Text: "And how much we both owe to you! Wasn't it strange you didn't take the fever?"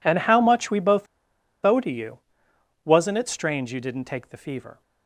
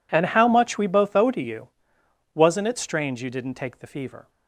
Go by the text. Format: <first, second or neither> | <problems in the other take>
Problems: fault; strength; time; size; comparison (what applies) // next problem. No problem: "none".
second | pauses between "both" and "owe"; noticeable; at 1.0 s; 0.57 s long